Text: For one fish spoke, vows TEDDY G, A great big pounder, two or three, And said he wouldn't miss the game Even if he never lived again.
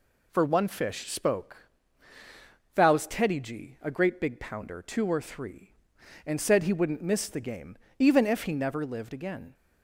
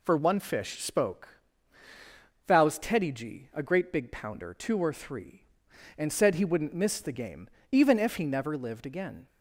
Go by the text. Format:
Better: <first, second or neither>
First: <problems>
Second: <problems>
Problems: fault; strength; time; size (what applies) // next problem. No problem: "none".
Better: neither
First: pauses between "game" and "Even"; slight; at 7.7 s; 0.23 s long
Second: pauses between "game" and "Even"; slight; at 7.4 s; 0.24 s long